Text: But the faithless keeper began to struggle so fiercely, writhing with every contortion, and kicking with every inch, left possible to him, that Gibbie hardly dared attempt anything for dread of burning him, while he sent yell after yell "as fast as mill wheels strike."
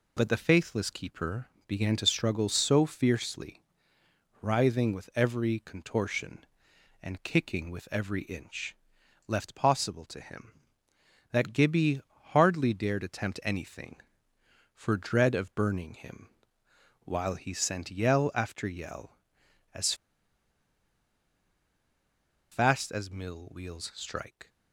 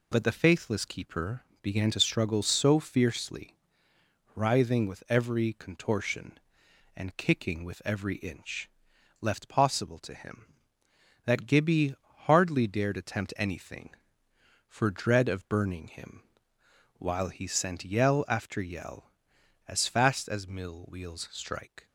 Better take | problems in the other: second | pauses between "keeper" and "began"; slight; at 1.4 s; 0.22 s long; slight in the second // pauses between "Gibbie" and "hardly"; slight; at 12.0 s; 0.28 s long; slight in the second // pauses between "as" and "fast"; strong; at 19.9 s; 2.5 s long

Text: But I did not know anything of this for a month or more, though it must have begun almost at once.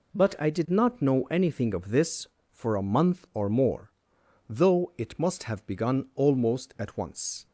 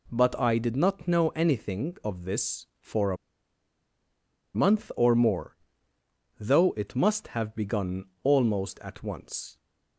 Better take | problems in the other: first | pauses between "a" and "month"; strong; at 3.1 s; 1.3 s long // pauses between "begun" and "almost"; slight; at 8.0 s; 0.18 s long

